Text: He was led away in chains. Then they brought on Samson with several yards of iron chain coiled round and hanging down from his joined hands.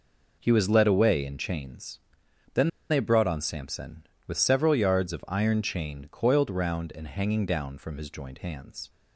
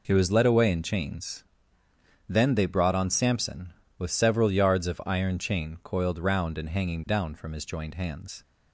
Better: second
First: pauses between "Then" and "they"; slight; at 2.6 s; 0.20 s long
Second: none

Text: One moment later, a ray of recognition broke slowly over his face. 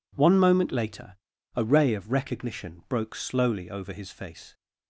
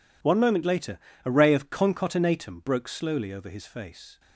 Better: first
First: none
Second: says "concatenatum" for "recognition"; at 1.7 s

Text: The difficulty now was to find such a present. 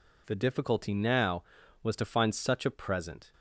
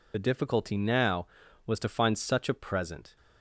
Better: first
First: none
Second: loses the start of "The"; at 0.1 s; 50 ms

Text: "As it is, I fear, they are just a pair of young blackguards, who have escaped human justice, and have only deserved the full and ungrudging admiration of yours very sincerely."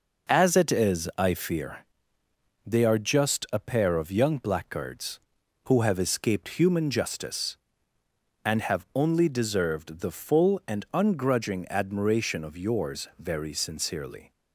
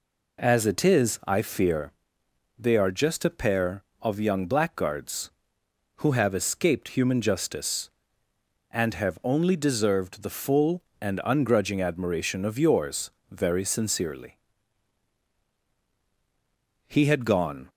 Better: first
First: none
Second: pauses between "yours" and "very"; slight; at 13.1 s; 0.18 s long // goes on to say "He had gone"; noticeable; from 16.8 s on; 0.82 s long

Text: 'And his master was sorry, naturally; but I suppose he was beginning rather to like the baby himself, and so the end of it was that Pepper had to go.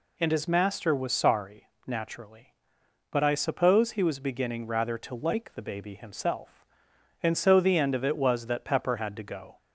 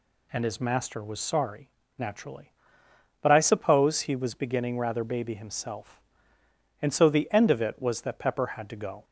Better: first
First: none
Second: skips "to like the"; at 5.0 s

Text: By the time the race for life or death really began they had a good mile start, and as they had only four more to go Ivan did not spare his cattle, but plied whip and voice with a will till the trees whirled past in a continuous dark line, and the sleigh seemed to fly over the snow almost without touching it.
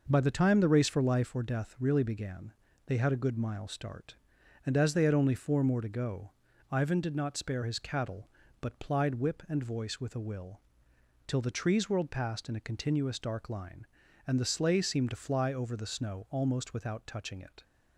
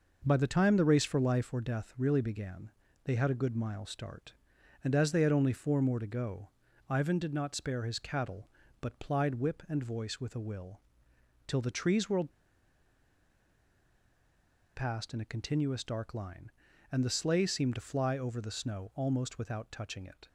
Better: first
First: pauses between "began" and "they"; slight; at 2.5 s; 0.34 s long // pauses between "go" and "Ivan"; at 6.3 s; 0.40 s long // pauses between "will" and "till"; noticeable; at 10.5 s; 0.68 s long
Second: pauses between "began" and "they"; slight; at 2.7 s; 0.34 s long // pauses between "go" and "Ivan"; at 6.4 s; 0.40 s long // pauses between "will" and "till"; noticeable; at 10.7 s; 0.68 s long // pauses between "whirled" and "past"; strong; at 12.3 s; 2.4 s long

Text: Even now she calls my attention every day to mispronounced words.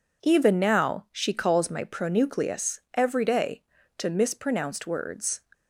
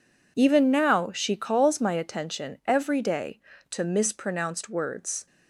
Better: second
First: says "pronucleus" for "attention"; at 1.8 s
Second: none

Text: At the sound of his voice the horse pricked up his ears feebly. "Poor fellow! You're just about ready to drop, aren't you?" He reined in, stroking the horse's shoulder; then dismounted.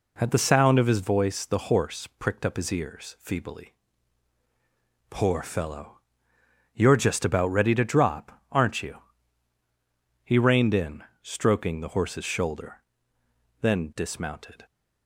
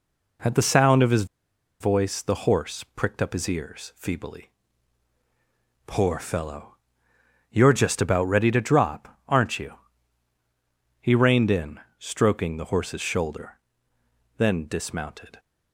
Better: first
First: none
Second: pauses between "his" and "voice"; noticeable; at 1.2 s; 0.55 s long

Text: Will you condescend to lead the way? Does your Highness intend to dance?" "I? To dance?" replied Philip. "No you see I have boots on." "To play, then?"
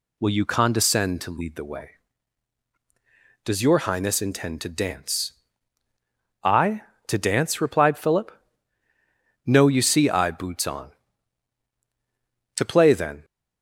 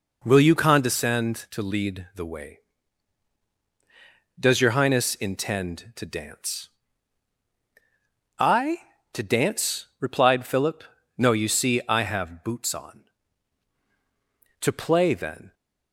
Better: second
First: skips "have"; at 10.3 s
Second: none

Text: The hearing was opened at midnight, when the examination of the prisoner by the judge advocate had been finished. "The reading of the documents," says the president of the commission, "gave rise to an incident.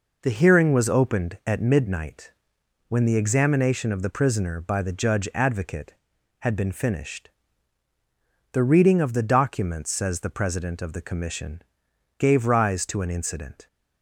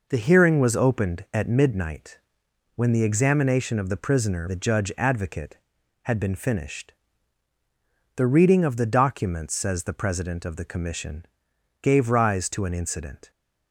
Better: first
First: none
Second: skips "by"; at 4.4 s

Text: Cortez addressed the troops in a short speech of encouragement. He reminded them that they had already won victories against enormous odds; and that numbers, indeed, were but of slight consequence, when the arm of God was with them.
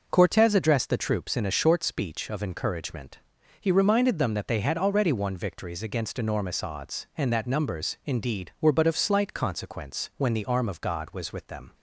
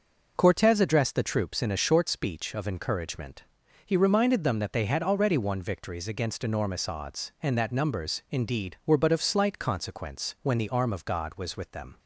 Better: neither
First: none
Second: none

